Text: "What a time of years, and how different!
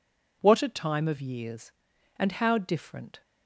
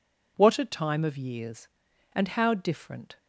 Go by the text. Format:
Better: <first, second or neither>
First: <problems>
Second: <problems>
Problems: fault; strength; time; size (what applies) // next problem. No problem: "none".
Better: neither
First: none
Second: none